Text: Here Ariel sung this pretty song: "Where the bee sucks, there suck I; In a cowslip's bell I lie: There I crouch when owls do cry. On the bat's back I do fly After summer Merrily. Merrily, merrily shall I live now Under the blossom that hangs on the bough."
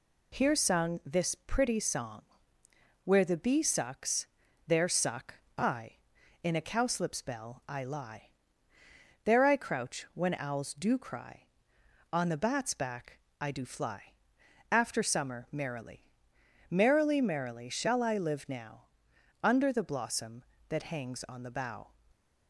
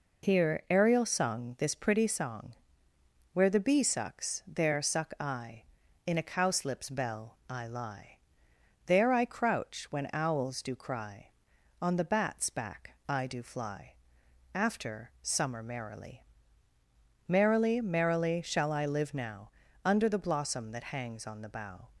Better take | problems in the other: second | skips "Ariel"; at 0.5 s // pauses between "suck" and "I"; slight; at 5.3 s; 0.24 s long // pauses between "back" and "I"; slight; at 13.1 s; 0.20 s long // pauses between "fly" and "After"; noticeable; at 14.1 s; 0.58 s long; noticeable in the second // pauses between "now" and "Under"; noticeable; at 18.8 s; 0.58 s long; slight in the second

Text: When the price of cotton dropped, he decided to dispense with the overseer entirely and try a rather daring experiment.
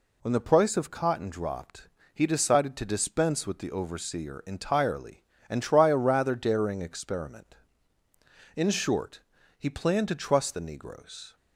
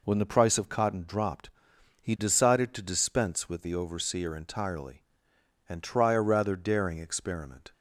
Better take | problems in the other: second | goes on to say "In short he planned to trust the Negroes"; strong; from 8.5 s on; 2.8 s long

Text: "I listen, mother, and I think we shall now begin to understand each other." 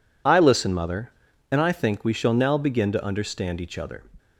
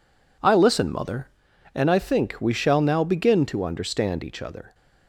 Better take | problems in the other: neither | none

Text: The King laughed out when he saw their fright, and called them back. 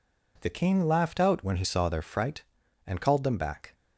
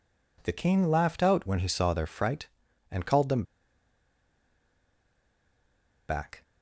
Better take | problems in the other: first | pauses between "them" and "back"; strong; at 3.4 s; 2.6 s long

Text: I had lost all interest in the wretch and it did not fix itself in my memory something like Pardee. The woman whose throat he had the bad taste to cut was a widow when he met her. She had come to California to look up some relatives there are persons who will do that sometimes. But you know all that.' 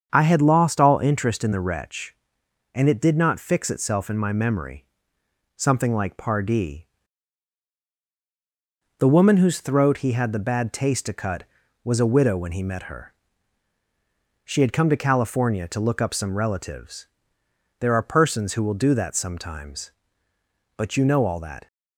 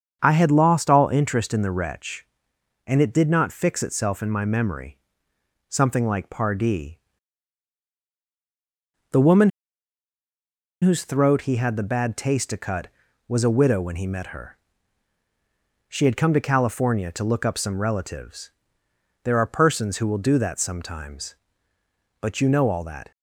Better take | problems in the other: first | starts louder than the rest; strong; until 1.2 s; 7.5 dB; strong in the first // pauses between "memory" and "something"; noticeable; at 4.9 s; 0.72 s long; noticeable in the first // pauses between "woman" and "whose"; strong; at 9.4 s; 1.3 s long // pauses between "relatives" and "there"; noticeable; at 18.5 s; 0.72 s long; noticeable in the first

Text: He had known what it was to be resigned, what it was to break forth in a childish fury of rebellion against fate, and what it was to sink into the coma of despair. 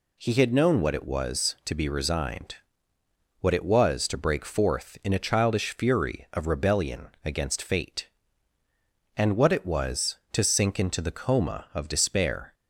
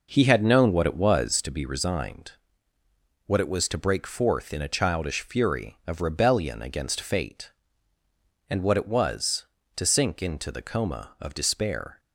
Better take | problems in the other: first | starts louder than the rest; noticeable; until 1.5 s; 5.5 dB

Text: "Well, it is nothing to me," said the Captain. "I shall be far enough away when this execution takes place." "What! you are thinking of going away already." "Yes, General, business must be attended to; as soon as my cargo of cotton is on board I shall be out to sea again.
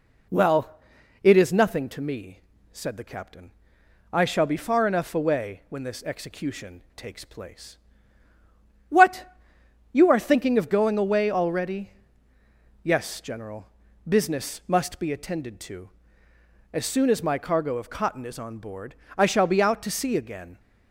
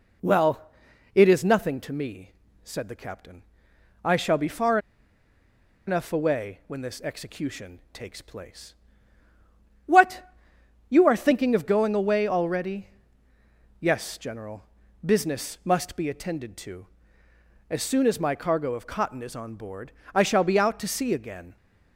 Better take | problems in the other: first | pauses between "far" and "enough"; at 4.7 s; 1.0 s long // pauses between "board" and "I"; slight; at 19.9 s; 0.24 s long; slight in the first

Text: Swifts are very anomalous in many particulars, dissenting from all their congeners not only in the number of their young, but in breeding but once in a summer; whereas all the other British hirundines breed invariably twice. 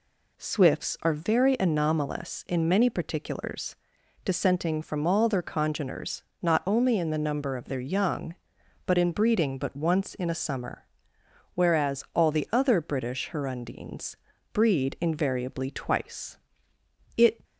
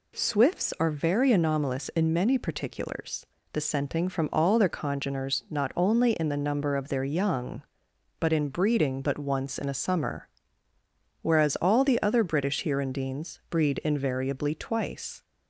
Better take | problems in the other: second | pauses between "congeners" and "not"; slight; at 6.2 s; 0.18 s long // pauses between "hirundines" and "breed"; at 14.1 s; 0.38 s long // goes on to say "It"; slight; from 17.1 s on; 0.28 s long

